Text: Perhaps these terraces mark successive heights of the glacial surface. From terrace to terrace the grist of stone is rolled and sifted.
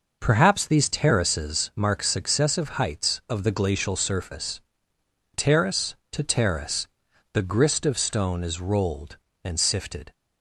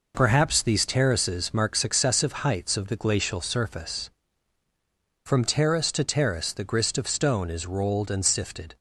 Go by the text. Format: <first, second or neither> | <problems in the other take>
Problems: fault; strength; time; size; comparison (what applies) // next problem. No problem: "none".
second | skips "From"; at 4.9 s // pauses between "terrace" and "the"; noticeable; at 6.8 s; 0.46 s long